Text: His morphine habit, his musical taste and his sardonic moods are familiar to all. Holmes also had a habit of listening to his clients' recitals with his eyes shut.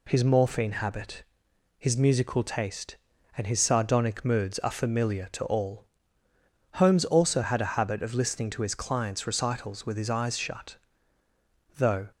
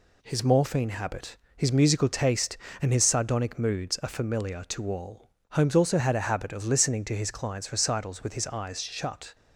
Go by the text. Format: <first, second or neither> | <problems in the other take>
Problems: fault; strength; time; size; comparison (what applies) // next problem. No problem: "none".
second | goes on to say "Though"; slight; from 11.7 s on; 0.34 s long